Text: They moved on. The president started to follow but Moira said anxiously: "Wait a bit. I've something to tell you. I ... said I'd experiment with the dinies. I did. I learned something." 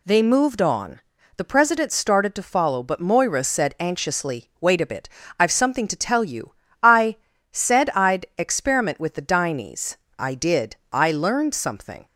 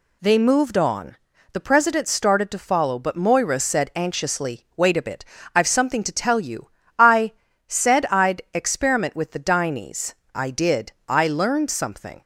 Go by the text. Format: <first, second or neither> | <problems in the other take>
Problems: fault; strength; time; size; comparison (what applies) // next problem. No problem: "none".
neither | none